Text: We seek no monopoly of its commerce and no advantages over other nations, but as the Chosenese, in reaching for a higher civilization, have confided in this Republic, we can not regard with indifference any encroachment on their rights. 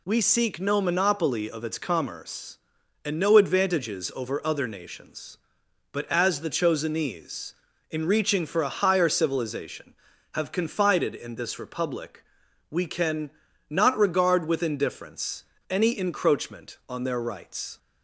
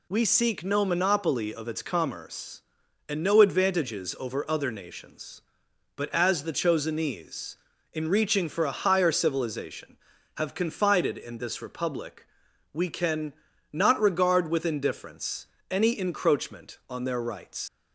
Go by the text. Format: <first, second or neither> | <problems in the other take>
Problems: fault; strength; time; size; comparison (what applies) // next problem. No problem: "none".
first | pauses between "can" and "not"; at 13.3 s; 0.38 s long; also in the first // pauses between "indifference" and "any"; slight; at 15.4 s; 0.24 s long; slight in the first // leaves "rights" unfinished; at 17.6 s; 105 ms